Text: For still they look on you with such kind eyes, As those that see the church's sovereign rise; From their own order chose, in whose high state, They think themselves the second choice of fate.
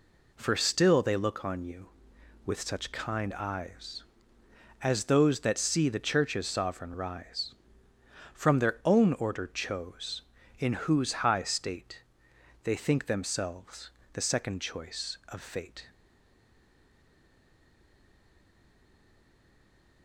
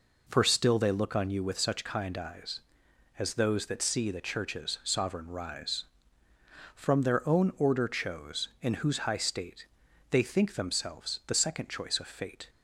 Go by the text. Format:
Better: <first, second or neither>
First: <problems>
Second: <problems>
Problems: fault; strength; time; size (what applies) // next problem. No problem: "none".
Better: second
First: pauses between "themselves" and "the"; slight; at 13.8 s; 0.24 s long // stays silent after the last word; strong; from 15.8 s on; 4.2 s long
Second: none